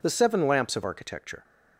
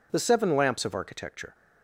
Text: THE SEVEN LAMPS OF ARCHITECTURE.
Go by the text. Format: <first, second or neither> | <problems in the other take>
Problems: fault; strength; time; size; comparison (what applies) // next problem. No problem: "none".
neither | none